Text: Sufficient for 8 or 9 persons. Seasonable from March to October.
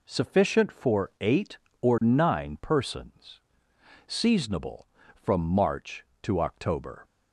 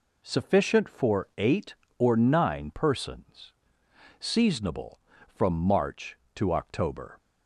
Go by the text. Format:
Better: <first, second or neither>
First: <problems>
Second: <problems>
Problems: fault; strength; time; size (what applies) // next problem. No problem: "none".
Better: neither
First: none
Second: none